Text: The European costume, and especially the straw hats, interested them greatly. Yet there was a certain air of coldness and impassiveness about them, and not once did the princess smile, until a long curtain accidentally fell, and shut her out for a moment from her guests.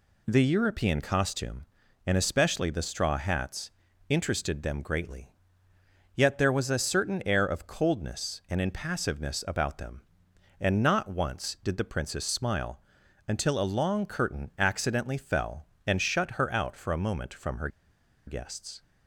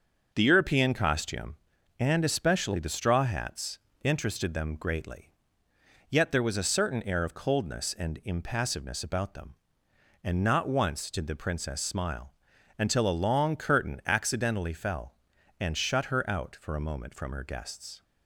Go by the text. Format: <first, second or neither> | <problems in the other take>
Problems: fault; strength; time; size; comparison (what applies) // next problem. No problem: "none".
second | pauses between "her" and "guests"; noticeable; at 17.6 s; 0.58 s long